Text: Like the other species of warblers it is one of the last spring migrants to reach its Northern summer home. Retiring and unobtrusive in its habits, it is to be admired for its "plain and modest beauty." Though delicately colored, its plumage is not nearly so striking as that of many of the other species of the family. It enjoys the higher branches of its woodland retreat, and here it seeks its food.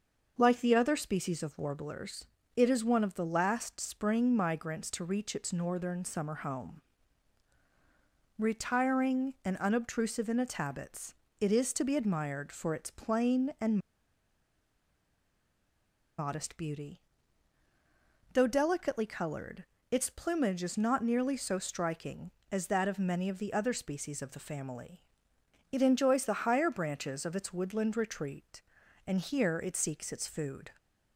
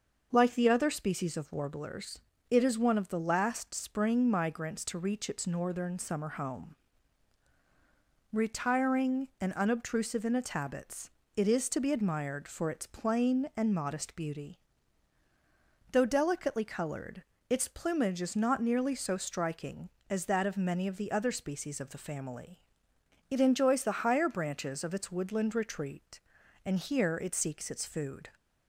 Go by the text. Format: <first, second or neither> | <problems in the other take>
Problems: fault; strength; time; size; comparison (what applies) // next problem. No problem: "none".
second | starts louder than the rest; noticeable; until 1.3 s; 6 dB; noticeable in the second // pauses between "warblers" and "it"; slight; at 2.2 s; 0.30 s long; slight in the second // pauses between "and" and "modest"; strong; at 13.7 s; 2.4 s long